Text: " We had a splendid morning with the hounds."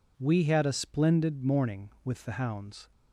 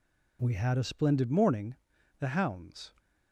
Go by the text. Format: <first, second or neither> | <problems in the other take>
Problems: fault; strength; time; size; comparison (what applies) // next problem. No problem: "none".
first | skips "with"; at 1.9 s